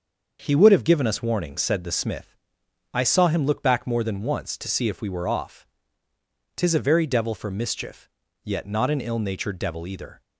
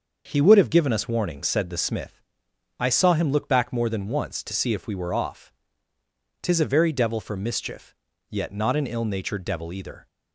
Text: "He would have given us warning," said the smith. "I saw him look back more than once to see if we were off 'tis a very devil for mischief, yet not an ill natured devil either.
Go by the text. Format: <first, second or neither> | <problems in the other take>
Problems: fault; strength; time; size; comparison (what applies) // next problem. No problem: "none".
neither | starts louder than the rest; the same in both // pauses between "off" and "tis"; noticeable; the same in both